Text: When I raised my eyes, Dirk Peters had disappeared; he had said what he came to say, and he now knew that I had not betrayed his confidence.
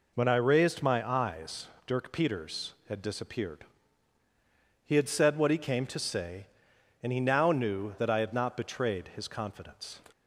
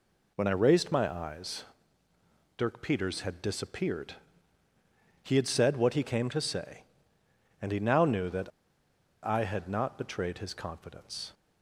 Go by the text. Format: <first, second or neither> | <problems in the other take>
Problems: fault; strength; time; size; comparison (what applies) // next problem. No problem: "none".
first | pauses between "that" and "I"; noticeable; at 8.5 s; 0.72 s long